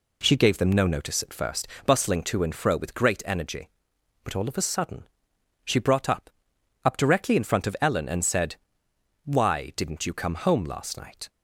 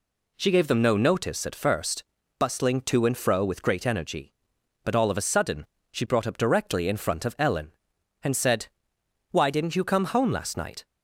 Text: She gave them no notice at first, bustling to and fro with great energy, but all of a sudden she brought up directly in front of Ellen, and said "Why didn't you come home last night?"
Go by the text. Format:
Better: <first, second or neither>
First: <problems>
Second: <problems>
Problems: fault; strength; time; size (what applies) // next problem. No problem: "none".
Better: second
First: pauses between "sudden" and "she"; noticeable; at 5.0 s; 0.54 s long // says "up" twice; at 6.8 s // pauses between "said" and "Why"; noticeable; at 8.5 s; 0.72 s long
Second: pauses between "sudden" and "she"; slight; at 5.6 s; 0.26 s long // pauses between "said" and "Why"; noticeable; at 8.6 s; 0.64 s long